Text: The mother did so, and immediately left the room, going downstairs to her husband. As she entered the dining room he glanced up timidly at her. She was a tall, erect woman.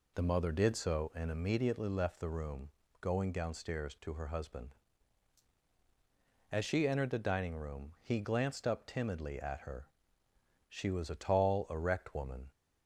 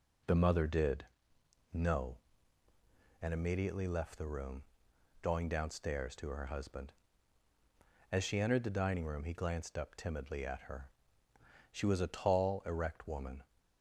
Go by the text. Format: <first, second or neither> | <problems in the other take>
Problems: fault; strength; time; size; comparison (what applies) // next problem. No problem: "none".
first | says "no" for "so"; at 1.7 s